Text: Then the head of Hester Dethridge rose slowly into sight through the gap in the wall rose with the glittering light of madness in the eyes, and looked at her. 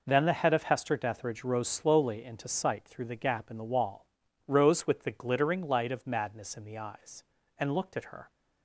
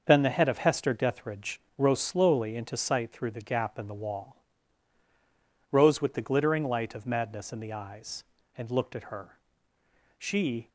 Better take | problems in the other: first | starts louder than the rest; until 1.0 s; 6.5 dB // pauses between "Dethridge" and "rose"; slight; at 1.6 s; 0.18 s long // pauses between "wall" and "rose"; strong; at 4.3 s; 1.3 s long; also in the first // goes on to say "She"; from 10.1 s on; 0.50 s long

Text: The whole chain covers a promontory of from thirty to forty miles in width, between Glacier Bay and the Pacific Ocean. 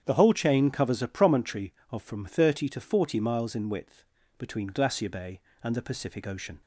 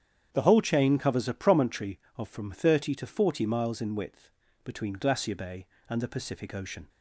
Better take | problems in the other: neither | starts louder than the rest; strong; the same in both

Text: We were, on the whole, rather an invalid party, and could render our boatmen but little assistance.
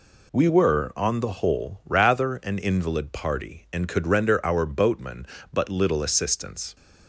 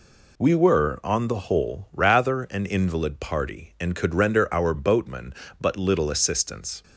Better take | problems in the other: neither | none

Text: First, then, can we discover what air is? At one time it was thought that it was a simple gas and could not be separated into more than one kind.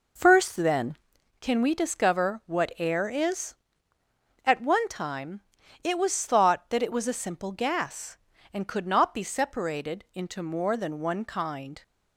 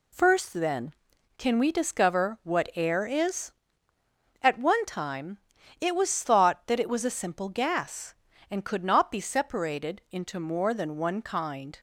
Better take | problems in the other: second | starts louder than the rest; noticeable; until 1.1 s; 4.5 dB // pauses between "time" and "it"; at 5.4 s; 0.42 s long; also in the second

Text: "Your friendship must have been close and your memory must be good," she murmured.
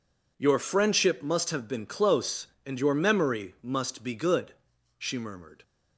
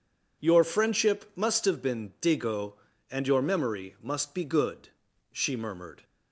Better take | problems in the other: first | says "digo" for "close"; at 2.2 s

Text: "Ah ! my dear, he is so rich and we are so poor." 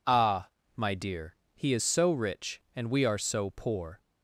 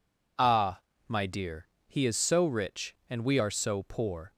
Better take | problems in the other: neither | none

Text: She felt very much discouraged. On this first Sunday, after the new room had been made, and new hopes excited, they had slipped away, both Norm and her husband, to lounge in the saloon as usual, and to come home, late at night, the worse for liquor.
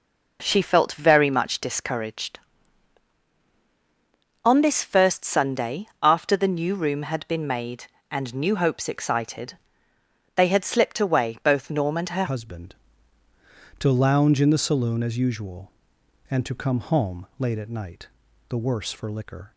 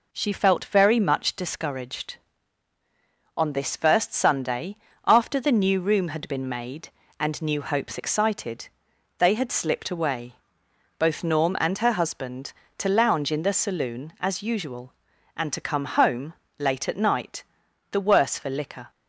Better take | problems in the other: second | changes voice at "husband"; from 12.2 s on; 7.3 s long

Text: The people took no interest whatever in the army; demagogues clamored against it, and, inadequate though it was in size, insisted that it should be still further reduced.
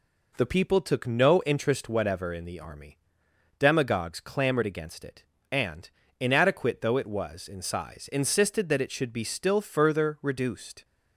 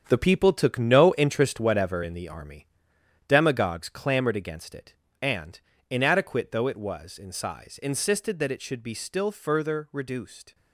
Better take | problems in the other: first | gets quieter; strong; throughout; 9.5 dB

